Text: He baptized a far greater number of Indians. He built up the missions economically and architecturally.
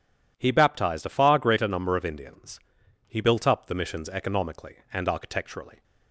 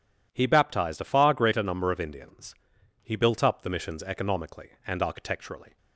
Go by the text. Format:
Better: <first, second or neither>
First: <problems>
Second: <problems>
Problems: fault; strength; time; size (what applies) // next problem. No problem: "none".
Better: neither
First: none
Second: none